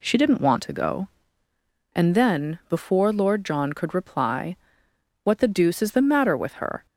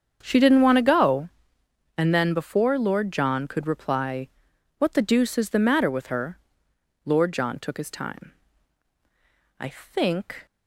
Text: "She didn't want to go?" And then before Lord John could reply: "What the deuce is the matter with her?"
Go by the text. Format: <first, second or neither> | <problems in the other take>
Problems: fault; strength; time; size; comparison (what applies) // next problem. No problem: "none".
first | starts louder than the rest; strong; until 1.2 s; 7.5 dB // goes on to say "Lord John took his time I think"; strong; from 7.0 s on; 3.4 s long